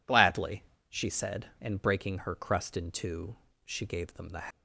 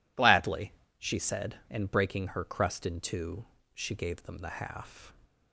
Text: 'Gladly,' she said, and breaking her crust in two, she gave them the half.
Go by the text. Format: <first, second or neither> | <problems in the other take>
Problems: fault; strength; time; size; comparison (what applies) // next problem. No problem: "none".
second | stops before "half"; at 4.5 s